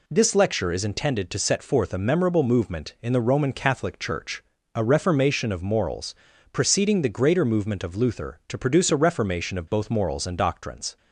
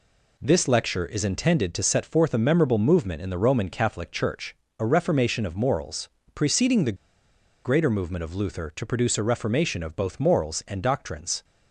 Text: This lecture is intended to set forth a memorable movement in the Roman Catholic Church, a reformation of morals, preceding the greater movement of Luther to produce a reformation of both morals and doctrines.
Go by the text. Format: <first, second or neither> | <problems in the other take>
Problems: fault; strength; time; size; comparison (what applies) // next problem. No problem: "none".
first | pauses between "the" and "greater"; noticeable; at 6.9 s; 0.69 s long